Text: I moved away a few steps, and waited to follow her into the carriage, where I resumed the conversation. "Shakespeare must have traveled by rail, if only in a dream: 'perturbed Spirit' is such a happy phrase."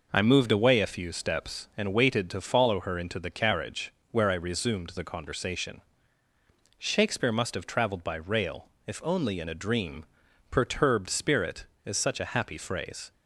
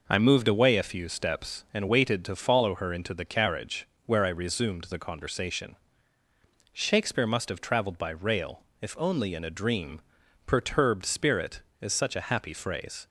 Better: neither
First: none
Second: none

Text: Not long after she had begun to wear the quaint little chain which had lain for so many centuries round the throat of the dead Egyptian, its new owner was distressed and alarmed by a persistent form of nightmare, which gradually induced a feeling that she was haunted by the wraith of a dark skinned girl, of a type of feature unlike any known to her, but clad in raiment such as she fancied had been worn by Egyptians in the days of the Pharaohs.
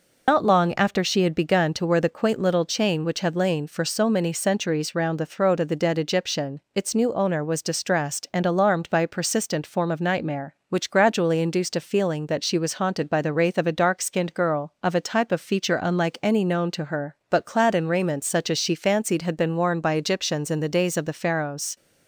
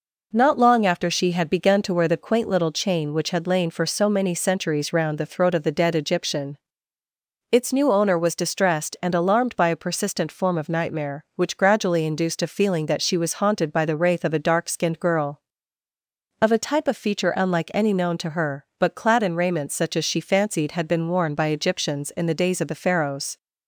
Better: second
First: loses the start of "Not"; at 0.2 s; 135 ms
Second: none

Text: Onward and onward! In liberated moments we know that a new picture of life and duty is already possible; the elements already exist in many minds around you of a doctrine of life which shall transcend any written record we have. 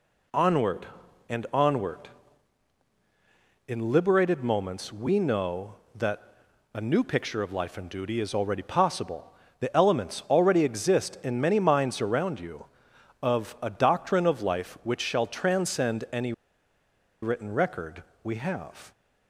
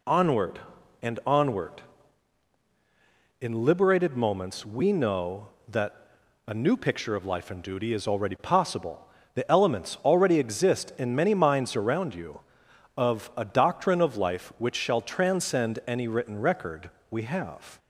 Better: second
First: pauses between "that" and "a"; noticeable; at 6.2 s; 0.50 s long // pauses between "any" and "written"; noticeable; at 16.3 s; 0.90 s long // pauses between "record" and "we"; slight; at 18.0 s; 0.18 s long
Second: pauses between "that" and "a"; noticeable; at 5.9 s; 0.50 s long // pauses between "record" and "we"; slight; at 16.9 s; 0.18 s long

